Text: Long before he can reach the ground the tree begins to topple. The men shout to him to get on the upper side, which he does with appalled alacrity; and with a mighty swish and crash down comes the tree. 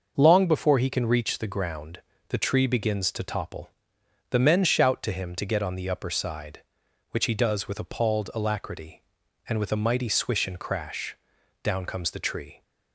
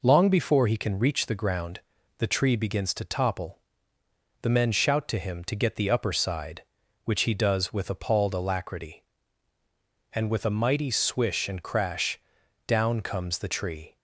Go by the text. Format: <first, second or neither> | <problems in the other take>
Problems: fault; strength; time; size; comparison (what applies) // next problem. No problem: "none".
first | pauses between "ground" and "the"; at 1.8 s; 0.38 s long; slight in the first // skips "on"; at 5.7 s // pauses between "crash" and "down"; noticeable; at 12.2 s; 0.48 s long; also in the first